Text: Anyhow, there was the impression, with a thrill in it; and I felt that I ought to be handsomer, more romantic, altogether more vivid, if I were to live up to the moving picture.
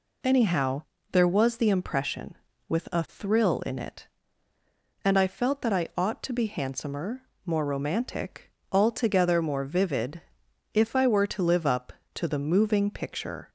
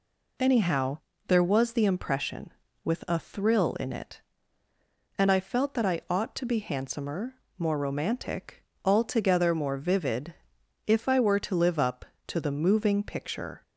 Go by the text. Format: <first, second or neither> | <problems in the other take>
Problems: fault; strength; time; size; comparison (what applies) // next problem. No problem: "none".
neither | none